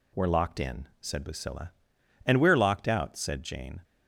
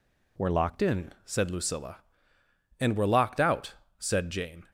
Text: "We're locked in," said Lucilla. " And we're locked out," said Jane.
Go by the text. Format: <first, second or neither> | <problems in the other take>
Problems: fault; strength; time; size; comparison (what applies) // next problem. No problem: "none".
first | changes voice at "in"; from 0.8 s on; 3.8 s long